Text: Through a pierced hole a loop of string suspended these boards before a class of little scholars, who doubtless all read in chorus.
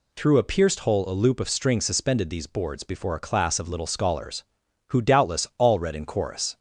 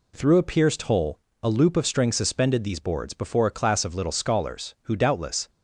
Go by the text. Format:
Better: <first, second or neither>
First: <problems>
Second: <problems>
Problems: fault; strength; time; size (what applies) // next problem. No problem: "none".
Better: first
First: none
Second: pauses between "hole" and "a"; slight; at 1.1 s; 0.24 s long // stops before "all read in chorus"; at 5.4 s